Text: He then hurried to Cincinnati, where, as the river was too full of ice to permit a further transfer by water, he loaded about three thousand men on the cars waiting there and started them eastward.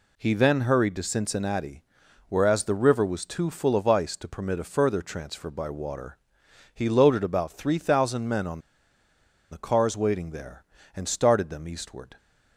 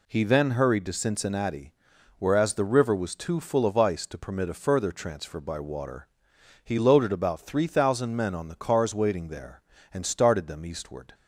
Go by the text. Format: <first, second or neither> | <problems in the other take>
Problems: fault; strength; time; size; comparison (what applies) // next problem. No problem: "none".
second | pauses between "on" and "the"; noticeable; at 8.6 s; 0.90 s long